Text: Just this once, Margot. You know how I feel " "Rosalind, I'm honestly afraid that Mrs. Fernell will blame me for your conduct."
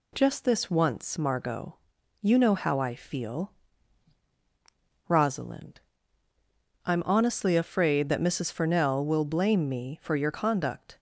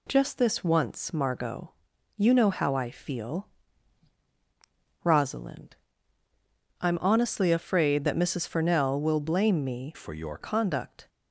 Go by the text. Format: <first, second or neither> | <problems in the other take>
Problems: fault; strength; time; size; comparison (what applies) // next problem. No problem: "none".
first | changes voice from "for" to "your"; from 9.9 to 10.3 s; 0.4 s long